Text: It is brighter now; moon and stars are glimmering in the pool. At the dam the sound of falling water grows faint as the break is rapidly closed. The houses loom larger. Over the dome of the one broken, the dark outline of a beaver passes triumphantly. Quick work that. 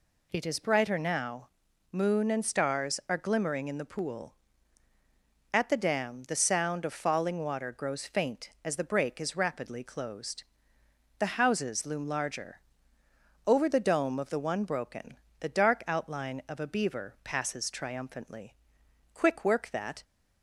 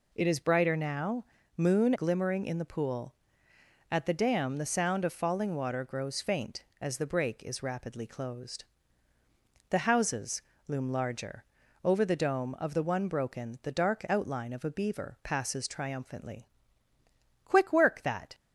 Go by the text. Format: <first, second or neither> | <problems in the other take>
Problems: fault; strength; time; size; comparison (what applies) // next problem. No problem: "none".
first | skips "and stars are"; at 1.9 s // pauses between "houses" and "loom"; slight; at 10.4 s; 0.24 s long